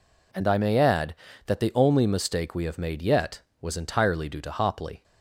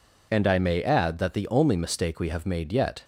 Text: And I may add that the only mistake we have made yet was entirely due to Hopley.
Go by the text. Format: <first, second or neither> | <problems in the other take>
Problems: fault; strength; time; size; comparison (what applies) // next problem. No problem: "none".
first | stops before "was entirely due to Hopley"; at 3.0 s